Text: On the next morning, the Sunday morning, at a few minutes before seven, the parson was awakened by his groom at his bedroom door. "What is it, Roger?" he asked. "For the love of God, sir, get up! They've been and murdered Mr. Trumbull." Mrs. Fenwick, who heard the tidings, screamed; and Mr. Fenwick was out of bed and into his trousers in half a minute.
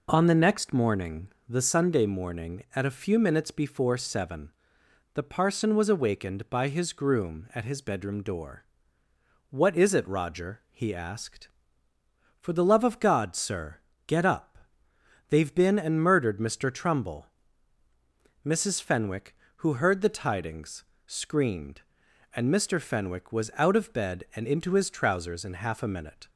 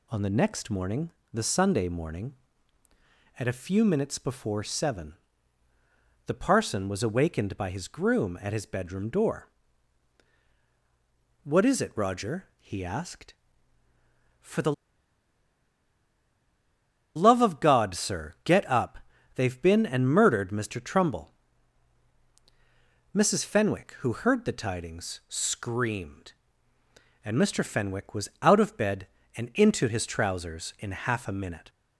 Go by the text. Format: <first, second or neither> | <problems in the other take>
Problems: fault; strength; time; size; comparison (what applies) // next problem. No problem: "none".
first | pauses between "the" and "love"; strong; at 14.7 s; 2.4 s long